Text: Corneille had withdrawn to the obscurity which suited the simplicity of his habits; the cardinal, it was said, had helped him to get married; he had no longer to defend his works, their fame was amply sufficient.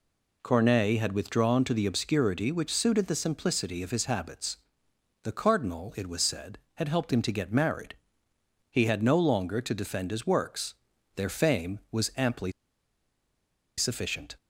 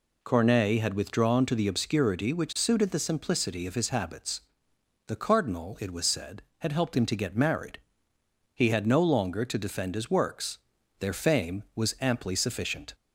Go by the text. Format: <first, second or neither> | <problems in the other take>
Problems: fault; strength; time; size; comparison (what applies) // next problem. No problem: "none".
second | pauses between "amply" and "sufficient"; strong; at 12.5 s; 1.2 s long